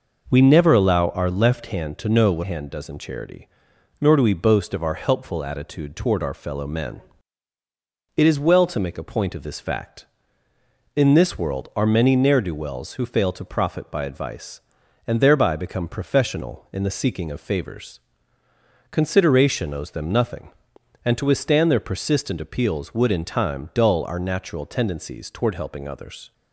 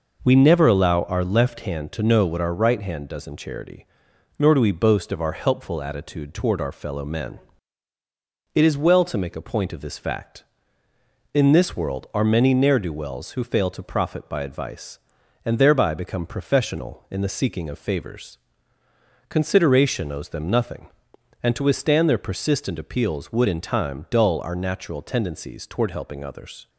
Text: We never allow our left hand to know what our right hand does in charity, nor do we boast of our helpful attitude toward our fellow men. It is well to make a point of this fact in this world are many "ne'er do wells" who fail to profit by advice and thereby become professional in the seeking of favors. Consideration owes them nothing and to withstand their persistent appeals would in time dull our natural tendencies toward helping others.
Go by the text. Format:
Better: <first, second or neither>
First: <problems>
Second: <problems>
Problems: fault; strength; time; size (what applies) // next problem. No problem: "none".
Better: second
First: skips "our right"; at 2.4 s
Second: none